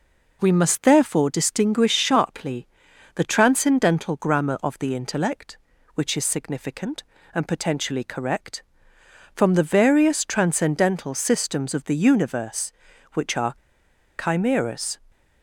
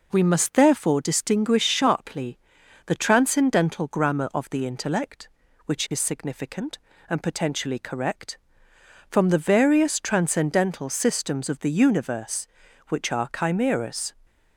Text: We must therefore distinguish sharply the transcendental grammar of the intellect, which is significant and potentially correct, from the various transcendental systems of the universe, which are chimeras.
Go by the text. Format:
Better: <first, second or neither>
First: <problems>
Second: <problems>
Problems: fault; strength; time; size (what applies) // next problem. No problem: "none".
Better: second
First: pauses between "sharply" and "the"; noticeable; at 2.6 s; 0.48 s long // pauses between "are" and "chimeras"; noticeable; at 13.5 s; 0.68 s long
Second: pauses between "sharply" and "the"; noticeable; at 2.3 s; 0.48 s long